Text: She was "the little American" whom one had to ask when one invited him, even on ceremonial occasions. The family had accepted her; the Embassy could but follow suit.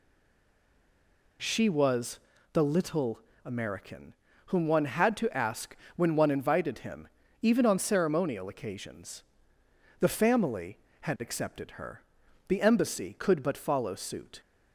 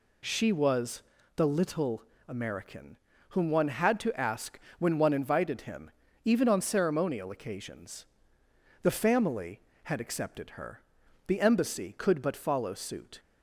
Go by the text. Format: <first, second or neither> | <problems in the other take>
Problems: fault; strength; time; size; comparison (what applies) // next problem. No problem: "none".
second | stays silent before the first word; noticeable; until 1.3 s; 1.3 s long // pauses between "was" and "the"; slight; at 2.1 s; 0.34 s long; slight in the second // pauses between "little" and "American"; slight; at 3.1 s; 0.28 s long; slight in the second // pauses between "American" and "whom"; at 4.1 s; 0.40 s long; also in the second // pauses between "ask" and "when"; slight; at 5.7 s; 0.22 s long; slight in the second